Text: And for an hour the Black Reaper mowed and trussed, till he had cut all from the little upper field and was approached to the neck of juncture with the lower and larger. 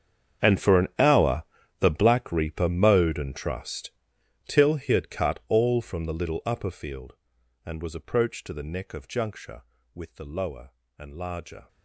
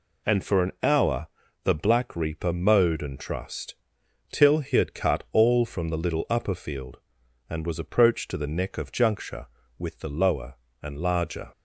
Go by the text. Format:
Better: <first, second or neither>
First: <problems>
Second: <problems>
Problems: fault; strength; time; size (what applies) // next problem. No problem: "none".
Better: second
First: gets quieter; strong; throughout; 18 dB // pauses between "hour" and "the"; slight; at 1.4 s; 0.36 s long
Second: pauses between "hour" and "the"; slight; at 1.2 s; 0.36 s long